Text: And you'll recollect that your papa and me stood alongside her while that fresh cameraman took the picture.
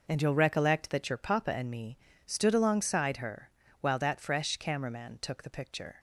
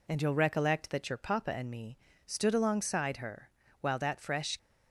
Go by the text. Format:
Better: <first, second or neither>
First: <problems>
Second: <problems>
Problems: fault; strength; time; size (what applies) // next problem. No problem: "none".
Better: first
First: pauses between "me" and "stood"; slight; at 1.9 s; 0.28 s long // pauses between "her" and "while"; slight; at 3.4 s; 0.32 s long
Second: pauses between "me" and "stood"; slight; at 1.9 s; 0.28 s long // pauses between "her" and "while"; slight; at 3.4 s; 0.32 s long // stops before "cameraman took the picture"; at 4.5 s